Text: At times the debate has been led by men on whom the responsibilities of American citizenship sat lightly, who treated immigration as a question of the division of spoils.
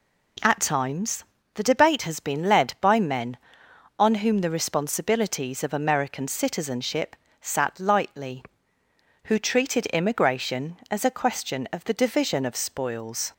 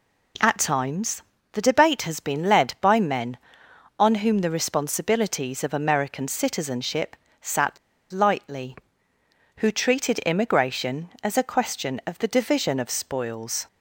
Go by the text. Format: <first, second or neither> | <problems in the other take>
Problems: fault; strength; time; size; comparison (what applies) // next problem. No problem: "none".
first | pauses between "times" and "the"; slight; at 1.2 s; 0.30 s long; slight in the first // pauses between "citizenship" and "sat"; slight; at 7.1 s; 0.24 s long; slight in the first // pauses between "sat" and "lightly"; slight; at 7.7 s; 0.35 s long